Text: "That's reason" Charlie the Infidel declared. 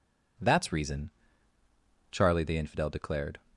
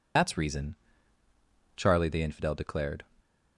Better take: first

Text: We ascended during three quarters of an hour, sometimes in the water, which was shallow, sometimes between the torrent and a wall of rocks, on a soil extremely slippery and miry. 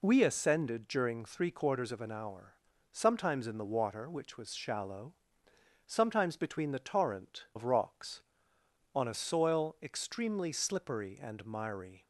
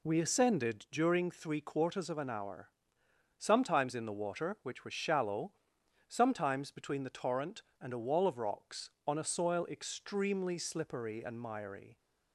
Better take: second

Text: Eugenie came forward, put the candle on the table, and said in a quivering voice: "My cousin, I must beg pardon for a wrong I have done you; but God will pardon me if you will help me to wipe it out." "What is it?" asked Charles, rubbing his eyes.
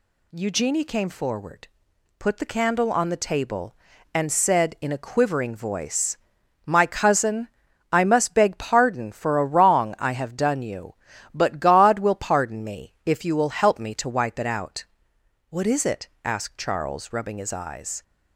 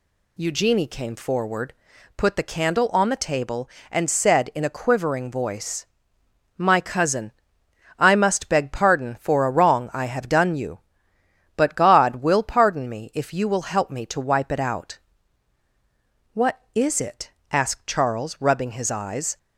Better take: neither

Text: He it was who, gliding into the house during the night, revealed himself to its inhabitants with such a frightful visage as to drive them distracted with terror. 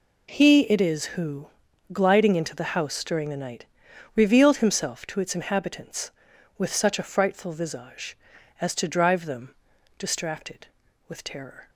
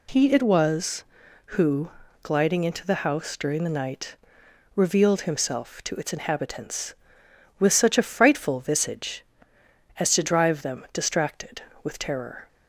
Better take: second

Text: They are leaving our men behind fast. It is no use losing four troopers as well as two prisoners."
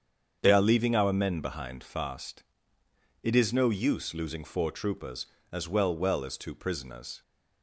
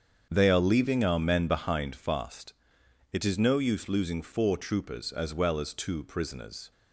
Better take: second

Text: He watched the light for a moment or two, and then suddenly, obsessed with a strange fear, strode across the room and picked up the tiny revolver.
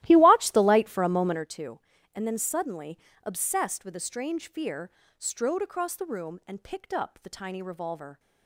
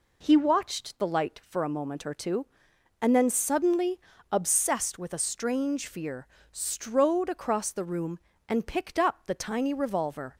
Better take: second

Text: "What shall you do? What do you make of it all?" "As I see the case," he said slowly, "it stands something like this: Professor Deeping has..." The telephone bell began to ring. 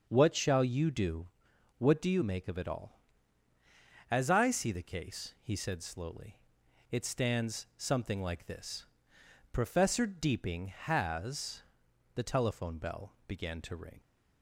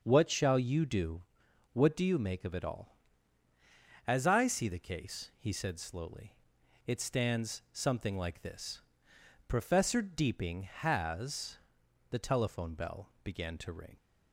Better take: neither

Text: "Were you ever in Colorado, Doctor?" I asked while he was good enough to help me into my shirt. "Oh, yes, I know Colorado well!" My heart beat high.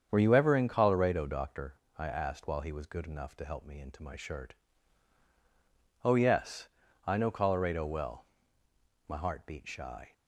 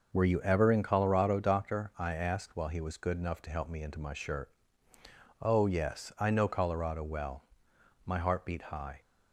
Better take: second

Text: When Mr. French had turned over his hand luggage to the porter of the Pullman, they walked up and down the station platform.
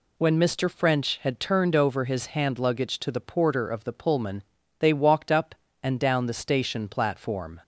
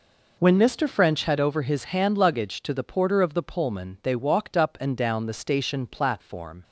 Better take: first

